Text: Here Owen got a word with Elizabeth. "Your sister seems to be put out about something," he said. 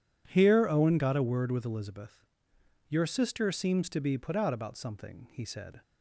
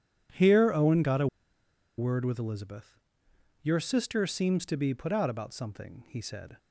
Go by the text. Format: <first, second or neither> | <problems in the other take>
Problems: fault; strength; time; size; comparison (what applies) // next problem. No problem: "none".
first | pauses between "a" and "word"; noticeable; at 1.2 s; 0.71 s long